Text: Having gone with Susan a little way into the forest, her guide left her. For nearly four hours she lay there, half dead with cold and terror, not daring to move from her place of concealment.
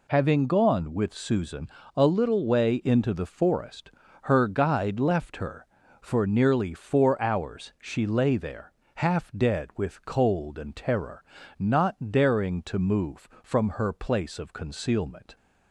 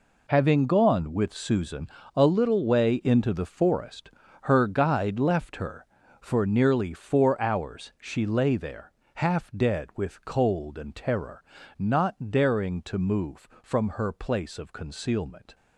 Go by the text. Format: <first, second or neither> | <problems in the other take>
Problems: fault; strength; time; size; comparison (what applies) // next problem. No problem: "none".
first | gets quieter; strong; throughout; 11.5 dB // pauses between "Susan" and "a"; slight; at 1.8 s; 0.26 s long; slight in the first